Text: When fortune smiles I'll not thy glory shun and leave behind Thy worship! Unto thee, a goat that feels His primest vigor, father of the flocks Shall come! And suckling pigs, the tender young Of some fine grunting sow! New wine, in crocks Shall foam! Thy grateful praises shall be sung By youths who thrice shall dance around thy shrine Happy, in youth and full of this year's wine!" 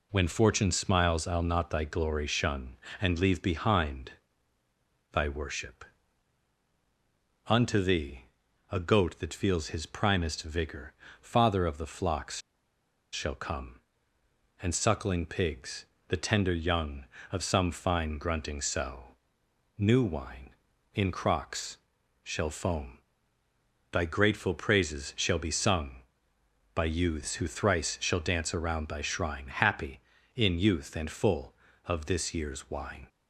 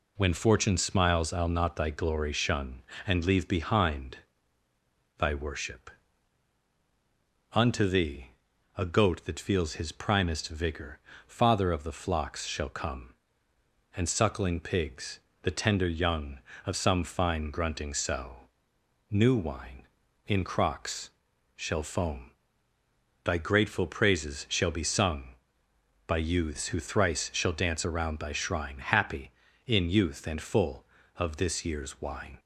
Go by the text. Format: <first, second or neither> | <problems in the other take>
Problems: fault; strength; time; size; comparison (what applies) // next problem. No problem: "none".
second | pauses between "behind" and "Thy"; at 4.1 s; 1.0 s long; also in the second // pauses between "flocks" and "Shall"; noticeable; at 12.3 s; 0.73 s long // pauses between "crocks" and "Shall"; noticeable; at 21.7 s; 0.46 s long; noticeable in the second